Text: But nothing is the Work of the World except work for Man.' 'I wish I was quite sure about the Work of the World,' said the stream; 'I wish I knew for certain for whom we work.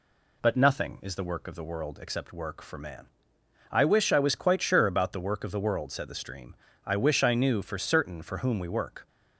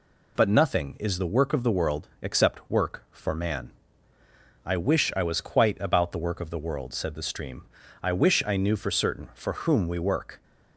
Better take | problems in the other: first | skips "sure"; at 5.7 s

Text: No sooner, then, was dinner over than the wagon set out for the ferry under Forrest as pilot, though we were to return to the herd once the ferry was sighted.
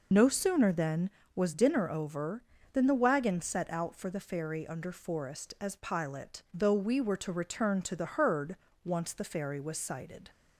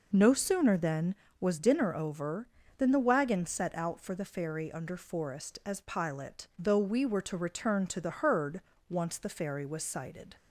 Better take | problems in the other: second | loses the start of "No"; at 0.1 s; 50 ms // pauses between "herd" and "once"; slight; at 8.5 s; 0.28 s long; slight in the second

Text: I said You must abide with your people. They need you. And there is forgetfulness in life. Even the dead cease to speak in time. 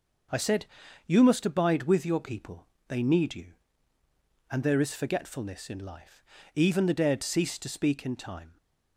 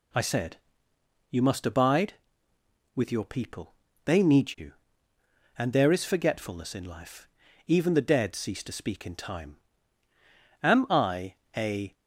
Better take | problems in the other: first | pauses between "said" and "You"; noticeable; at 0.5 s; 0.72 s long; also in the first // goes on to say "Am I a"; from 10.6 s on; 1.3 s long

